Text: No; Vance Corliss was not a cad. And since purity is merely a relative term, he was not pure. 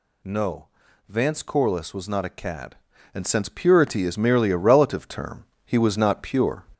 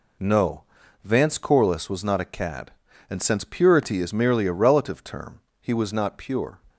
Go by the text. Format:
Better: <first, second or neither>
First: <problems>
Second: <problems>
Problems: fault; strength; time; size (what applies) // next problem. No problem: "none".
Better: second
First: gets louder; noticeable; throughout; 4.5 dB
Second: none